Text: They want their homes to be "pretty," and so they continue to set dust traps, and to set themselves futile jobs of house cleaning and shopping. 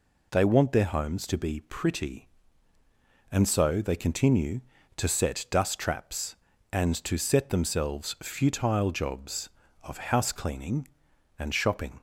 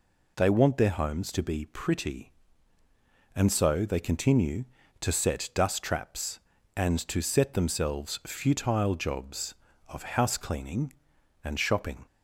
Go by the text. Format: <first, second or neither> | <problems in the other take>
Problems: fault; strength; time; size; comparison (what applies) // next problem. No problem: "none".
neither | none